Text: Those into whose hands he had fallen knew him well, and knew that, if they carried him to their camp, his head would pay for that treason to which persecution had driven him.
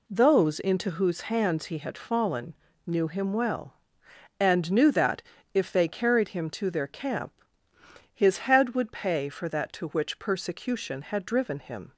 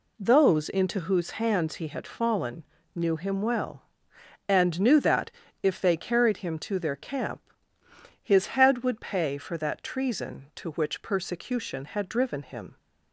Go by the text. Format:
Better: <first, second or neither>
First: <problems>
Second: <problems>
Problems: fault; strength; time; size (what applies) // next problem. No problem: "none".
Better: second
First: pauses between "fallen" and "knew"; slight; at 2.5 s; 0.32 s long // skips "treason"; at 9.7 s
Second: pauses between "fallen" and "knew"; slight; at 2.6 s; 0.31 s long